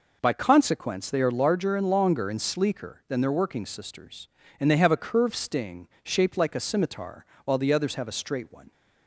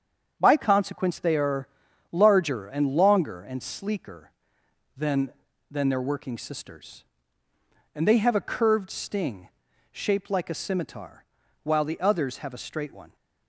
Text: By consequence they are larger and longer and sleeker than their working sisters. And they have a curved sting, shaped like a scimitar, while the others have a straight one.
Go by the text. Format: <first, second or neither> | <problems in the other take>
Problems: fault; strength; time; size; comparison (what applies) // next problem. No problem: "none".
first | starts louder than the rest; strong; until 1.4 s; 7.5 dB // pauses between "are" and "larger"; at 1.6 s; 0.44 s long // says "than" twice; at 5.7 s